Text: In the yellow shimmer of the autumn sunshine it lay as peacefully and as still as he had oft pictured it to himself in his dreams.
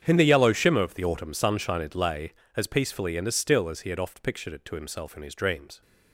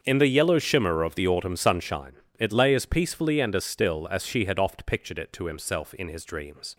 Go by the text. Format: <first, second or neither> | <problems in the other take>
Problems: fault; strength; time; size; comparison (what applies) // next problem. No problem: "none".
first | starts louder than the rest; until 1.0 s; 7 dB; strong in the first // pauses between "sunshine" and "it"; slight; at 2.1 s; 0.26 s long // says "she" for "he"; at 4.2 s